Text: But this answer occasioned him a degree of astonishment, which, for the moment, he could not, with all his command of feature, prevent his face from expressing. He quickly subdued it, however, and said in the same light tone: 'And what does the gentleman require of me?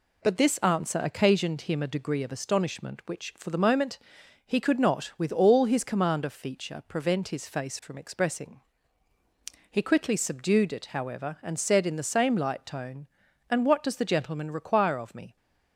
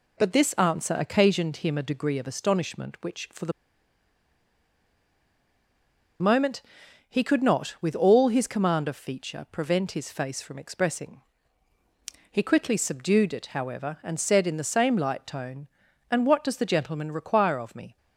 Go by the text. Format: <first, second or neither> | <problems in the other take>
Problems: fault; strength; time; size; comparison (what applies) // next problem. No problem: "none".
first | pauses between "the" and "moment"; strong; at 3.5 s; 2.6 s long